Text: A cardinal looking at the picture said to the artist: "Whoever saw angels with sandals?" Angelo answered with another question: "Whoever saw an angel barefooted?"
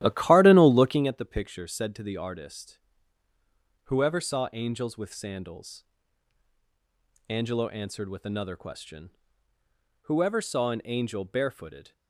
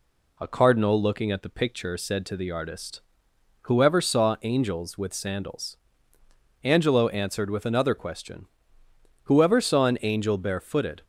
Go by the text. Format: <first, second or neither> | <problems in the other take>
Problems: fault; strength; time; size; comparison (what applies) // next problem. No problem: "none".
second | starts louder than the rest; strong; until 1.2 s; 13 dB